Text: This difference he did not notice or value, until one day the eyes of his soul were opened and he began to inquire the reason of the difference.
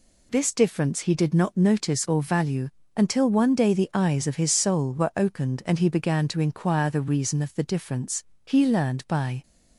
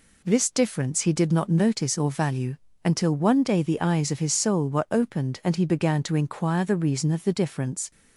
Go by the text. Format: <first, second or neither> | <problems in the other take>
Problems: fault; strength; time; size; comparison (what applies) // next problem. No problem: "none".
second | goes on to say "He learned by"; noticeable; from 8.4 s on; 0.96 s long